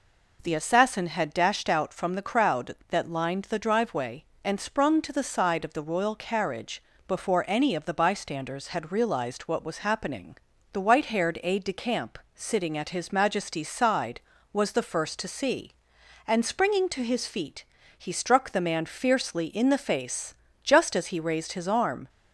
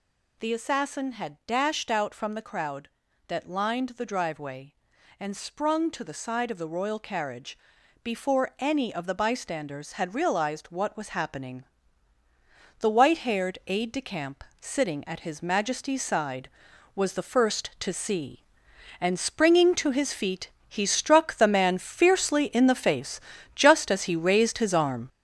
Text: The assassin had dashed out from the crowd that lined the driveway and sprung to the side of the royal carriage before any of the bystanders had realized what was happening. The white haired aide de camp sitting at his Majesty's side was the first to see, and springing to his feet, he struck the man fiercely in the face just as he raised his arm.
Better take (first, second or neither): first